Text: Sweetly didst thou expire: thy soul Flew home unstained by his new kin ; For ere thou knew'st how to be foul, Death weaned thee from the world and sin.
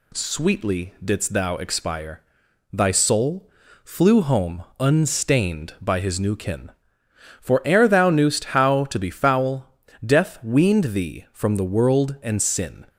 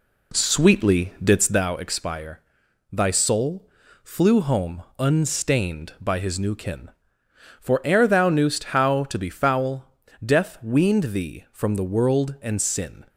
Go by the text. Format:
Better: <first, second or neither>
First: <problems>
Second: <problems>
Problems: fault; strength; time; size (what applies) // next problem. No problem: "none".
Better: first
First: pauses between "soul" and "Flew"; slight; at 3.4 s; 0.34 s long // pauses between "home" and "unstained"; slight; at 4.6 s; 0.16 s long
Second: starts louder than the rest; slight; until 1.8 s; 2.5 dB // pauses between "soul" and "Flew"; slight; at 3.6 s; 0.34 s long // pauses between "home" and "unstained"; slight; at 4.8 s; 0.16 s long